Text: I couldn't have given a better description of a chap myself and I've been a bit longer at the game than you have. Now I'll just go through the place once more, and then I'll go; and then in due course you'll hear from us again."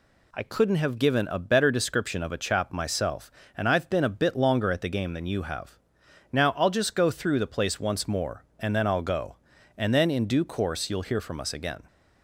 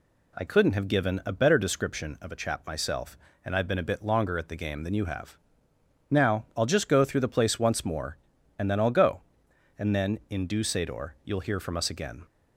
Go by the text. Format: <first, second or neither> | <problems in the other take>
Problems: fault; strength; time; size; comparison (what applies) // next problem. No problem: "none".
first | says "sador" for "course"; at 10.6 s